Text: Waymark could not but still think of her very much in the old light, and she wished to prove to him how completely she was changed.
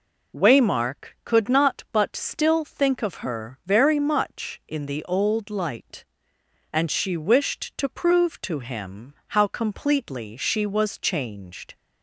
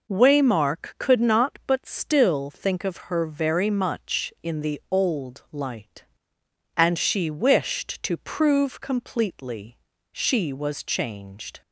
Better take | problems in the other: first | skips "to him how"; at 8.8 s // pauses between "completely" and "she"; slight; at 9.7 s; 0.34 s long

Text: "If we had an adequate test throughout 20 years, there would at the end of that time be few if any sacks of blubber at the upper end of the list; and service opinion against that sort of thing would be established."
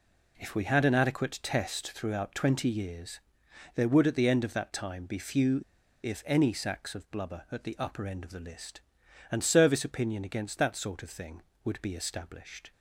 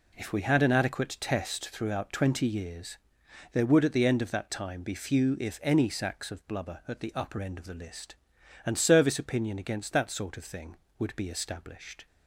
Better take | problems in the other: second | pauses between "few" and "if"; at 5.5 s; 0.43 s long

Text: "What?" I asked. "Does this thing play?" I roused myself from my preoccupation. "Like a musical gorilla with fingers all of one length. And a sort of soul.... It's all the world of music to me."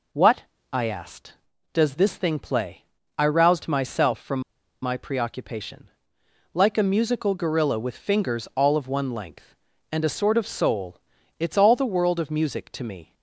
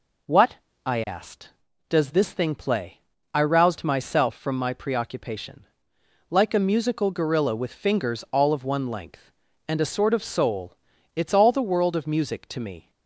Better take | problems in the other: second | pauses between "from" and "my"; at 4.4 s; 0.40 s long

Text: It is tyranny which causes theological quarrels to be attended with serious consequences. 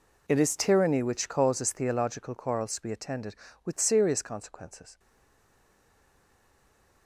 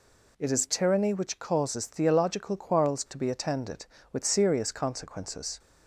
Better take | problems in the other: second | stays silent after the last word; noticeable; from 4.9 s on; 2.1 s long

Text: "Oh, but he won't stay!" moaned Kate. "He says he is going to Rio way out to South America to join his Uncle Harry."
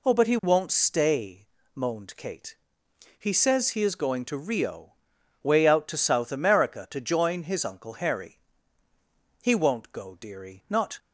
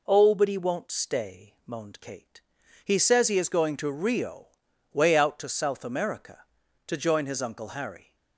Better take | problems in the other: second | pauses between "Rio" and "way"; noticeable; at 4.9 s; 0.50 s long; noticeable in the second // goes on to say "He won't go dearie not"; from 9.4 s on; 1.5 s long

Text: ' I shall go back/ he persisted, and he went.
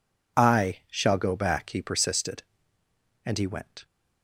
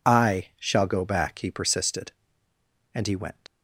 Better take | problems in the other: first | leaves "went" unfinished; at 3.4 s; 80 ms

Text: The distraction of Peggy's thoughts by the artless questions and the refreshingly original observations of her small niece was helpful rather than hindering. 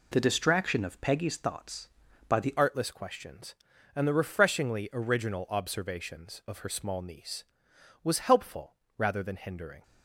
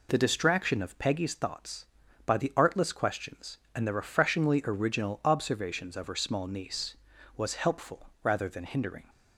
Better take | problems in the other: second | changes voice at "artless"; from 2.5 s on; 7.3 s long // pauses between "helpful" and "rather"; slight; at 8.7 s; 0.24 s long

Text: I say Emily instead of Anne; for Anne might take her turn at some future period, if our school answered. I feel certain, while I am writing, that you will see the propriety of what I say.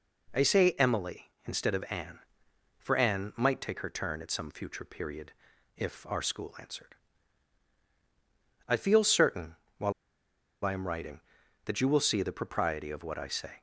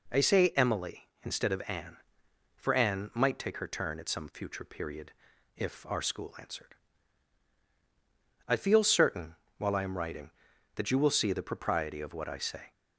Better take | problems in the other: second | pauses between "while" and "I"; noticeable; at 9.9 s; 0.71 s long

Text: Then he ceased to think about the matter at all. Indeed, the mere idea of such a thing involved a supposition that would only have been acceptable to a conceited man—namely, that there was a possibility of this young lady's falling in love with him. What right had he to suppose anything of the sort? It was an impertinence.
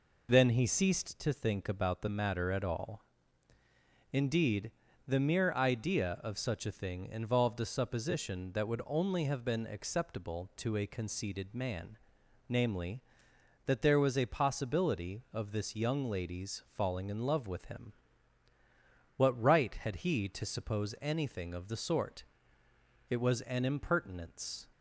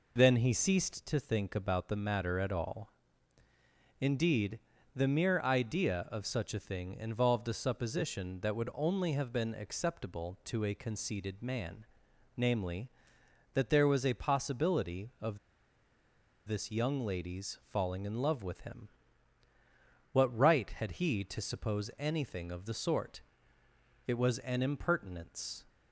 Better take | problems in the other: first | pauses between "of" and "this"; at 15.3 s; 1.0 s long // pauses between "lady's" and "falling"; slight; at 17.5 s; 0.16 s long; slight in the first

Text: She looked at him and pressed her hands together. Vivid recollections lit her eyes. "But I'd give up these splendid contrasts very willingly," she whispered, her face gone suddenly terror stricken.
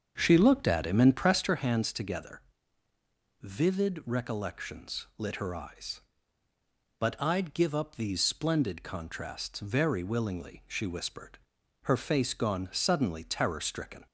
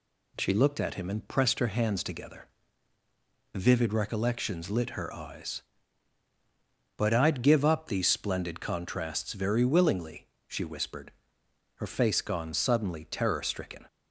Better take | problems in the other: second | starts louder than the rest; until 1.5 s; 7 dB

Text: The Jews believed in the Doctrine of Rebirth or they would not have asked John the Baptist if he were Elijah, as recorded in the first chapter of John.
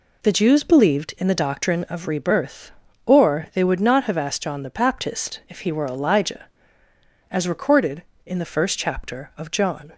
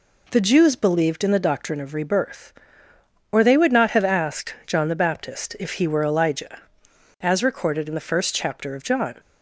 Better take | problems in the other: neither | none

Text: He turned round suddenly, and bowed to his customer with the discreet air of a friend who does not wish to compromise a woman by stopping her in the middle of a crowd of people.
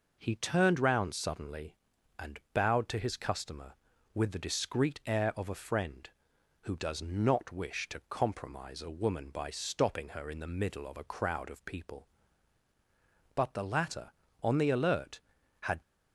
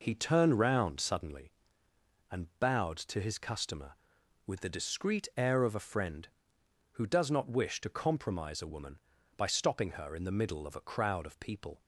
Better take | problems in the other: second | goes on to say "But the latter on the alert had"; strong; from 13.3 s on; 2.4 s long

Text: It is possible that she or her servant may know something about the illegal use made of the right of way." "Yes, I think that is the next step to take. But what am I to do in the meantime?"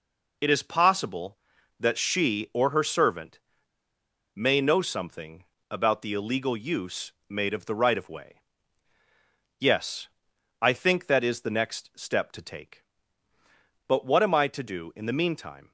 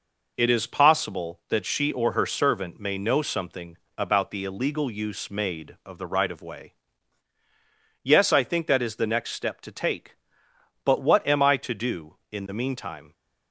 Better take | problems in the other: second | pauses between "servant" and "may"; noticeable; at 3.3 s; 0.96 s long // pauses between "something" and "about"; slight; at 5.4 s; 0.28 s long; slight in the second // pauses between "use" and "made"; slight; at 7.1 s; 0.16 s long

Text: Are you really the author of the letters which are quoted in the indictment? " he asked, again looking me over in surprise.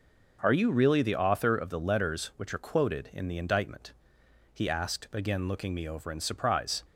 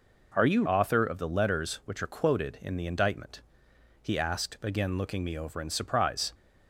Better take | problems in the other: first | skips "really the"; at 0.6 s

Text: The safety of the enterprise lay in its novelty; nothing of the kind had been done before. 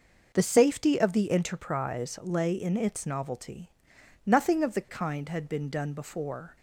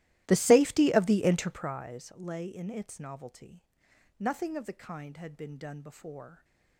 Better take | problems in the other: first | starts louder than the rest; strong; until 1.8 s; 15.5 dB

